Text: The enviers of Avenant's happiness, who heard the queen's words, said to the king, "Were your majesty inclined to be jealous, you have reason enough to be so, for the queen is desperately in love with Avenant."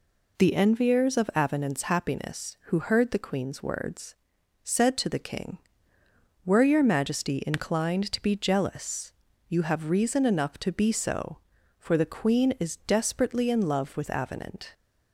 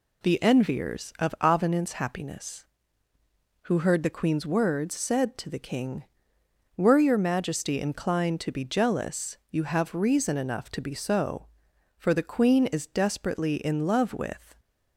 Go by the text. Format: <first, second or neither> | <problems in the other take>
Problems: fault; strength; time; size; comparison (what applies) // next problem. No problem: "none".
first | stops before "Avenant"; at 14.5 s